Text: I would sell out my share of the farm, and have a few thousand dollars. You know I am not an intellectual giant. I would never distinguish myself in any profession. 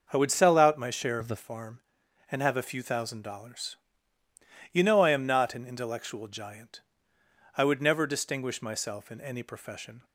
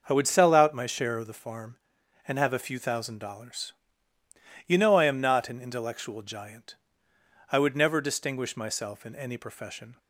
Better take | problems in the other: second | starts louder than the rest; noticeable; until 1.1 s; 6 dB; noticeable in the second // changes voice from "of" to "the"; from 1.2 to 1.3 s; 0.1 s long

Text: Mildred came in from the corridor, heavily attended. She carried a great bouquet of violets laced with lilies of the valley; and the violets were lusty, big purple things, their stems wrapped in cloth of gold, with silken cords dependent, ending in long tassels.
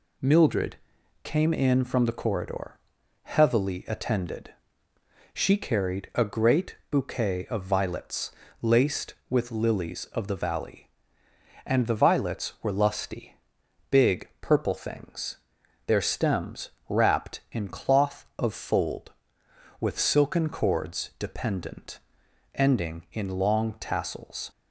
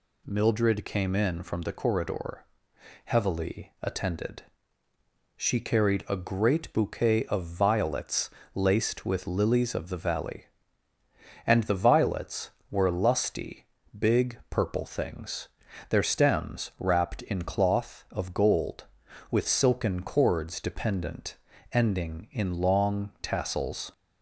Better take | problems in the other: second | pauses between "Mildred" and "came"; noticeable; at 0.7 s; 0.46 s long // pauses between "violets" and "laced"; slight; at 8.3 s; 0.28 s long; slight in the second // pauses between "stems" and "wrapped"; slight; at 16.7 s; 0.18 s long // says "fold" for "gold"; at 18.5 s

